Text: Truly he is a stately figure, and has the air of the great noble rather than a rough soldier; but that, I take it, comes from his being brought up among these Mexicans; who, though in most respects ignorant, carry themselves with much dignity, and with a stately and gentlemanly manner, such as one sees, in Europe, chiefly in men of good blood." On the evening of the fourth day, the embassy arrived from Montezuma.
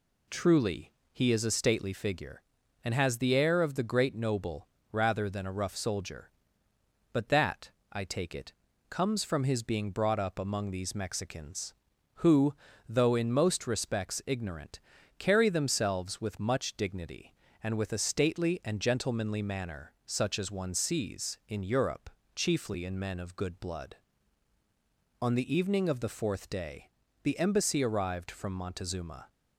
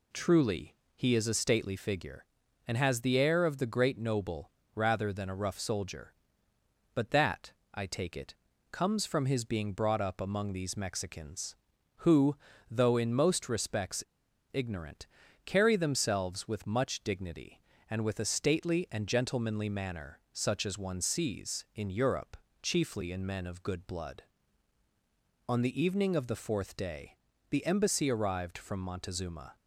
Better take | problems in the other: first | pauses between "Truly" and "he"; slight; at 0.7 s; 0.22 s long; slight in the first // pauses between "noble" and "rather"; slight; at 4.4 s; 0.24 s long; slight in the first // pauses between "respects" and "ignorant"; noticeable; at 14.0 s; 0.49 s long

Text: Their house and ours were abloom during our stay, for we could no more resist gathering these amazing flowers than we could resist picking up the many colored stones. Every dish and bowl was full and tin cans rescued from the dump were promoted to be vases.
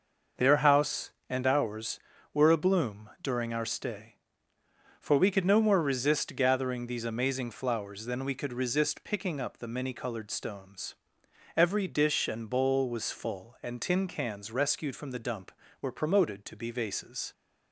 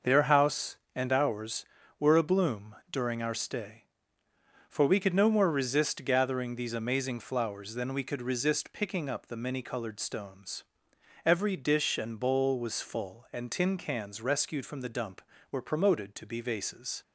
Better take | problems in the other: neither | starts louder than the rest; noticeable; the same in both // pauses between "abloom" and "during"; slight; the same in both

